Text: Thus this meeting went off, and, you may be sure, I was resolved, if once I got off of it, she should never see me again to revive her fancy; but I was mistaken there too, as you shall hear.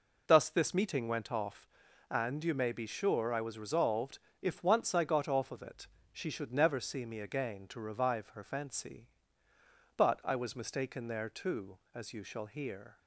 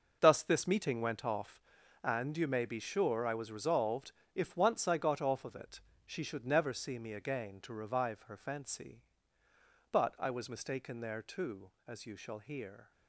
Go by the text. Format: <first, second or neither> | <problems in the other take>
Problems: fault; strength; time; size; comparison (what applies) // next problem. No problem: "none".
first | gets quieter; strong; throughout; 11.5 dB